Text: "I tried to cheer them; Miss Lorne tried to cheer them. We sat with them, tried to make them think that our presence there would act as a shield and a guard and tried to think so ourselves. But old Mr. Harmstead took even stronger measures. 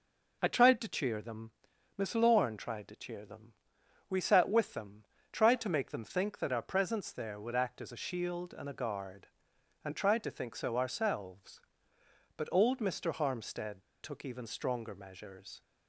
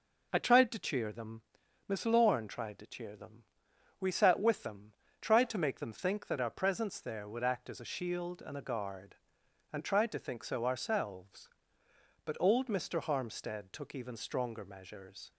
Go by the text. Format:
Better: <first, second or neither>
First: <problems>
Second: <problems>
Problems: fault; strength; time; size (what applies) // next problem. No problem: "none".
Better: second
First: pauses between "Harmstead" and "took"; slight; at 13.8 s; 0.18 s long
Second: none